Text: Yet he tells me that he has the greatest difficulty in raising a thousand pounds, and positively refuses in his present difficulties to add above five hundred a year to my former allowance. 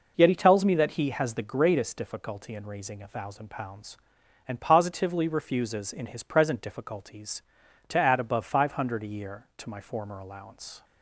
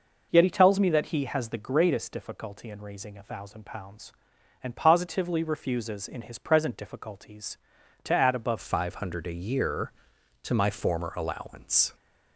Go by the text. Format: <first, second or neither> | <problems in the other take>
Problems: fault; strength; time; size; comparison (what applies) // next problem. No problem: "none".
first | changes voice at "five"; from 8.6 s on; 3.3 s long